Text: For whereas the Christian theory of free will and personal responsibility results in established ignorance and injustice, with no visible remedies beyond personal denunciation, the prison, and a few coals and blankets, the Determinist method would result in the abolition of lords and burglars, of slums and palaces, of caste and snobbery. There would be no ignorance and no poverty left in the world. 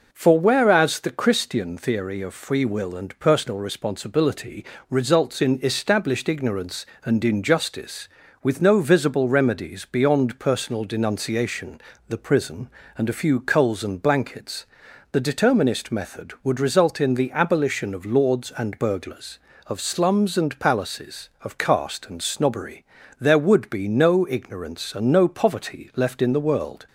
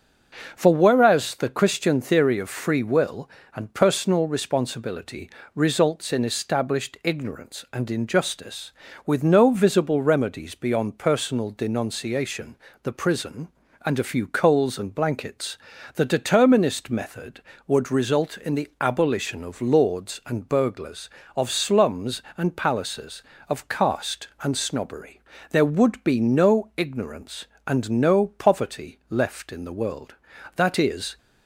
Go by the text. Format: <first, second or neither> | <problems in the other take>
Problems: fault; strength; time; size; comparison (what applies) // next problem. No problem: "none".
first | starts louder than the rest; noticeable; until 1.5 s; 6 dB // pauses between "responsibility" and "results"; slight; at 5.2 s; 0.26 s long; slight in the first // goes on to say "That is"; noticeable; from 30.5 s on; 0.62 s long